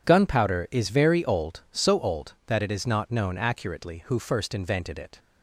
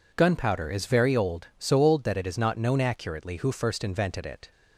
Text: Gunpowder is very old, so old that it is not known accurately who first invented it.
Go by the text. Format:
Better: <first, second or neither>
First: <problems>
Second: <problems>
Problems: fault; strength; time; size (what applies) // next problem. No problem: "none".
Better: neither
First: none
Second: none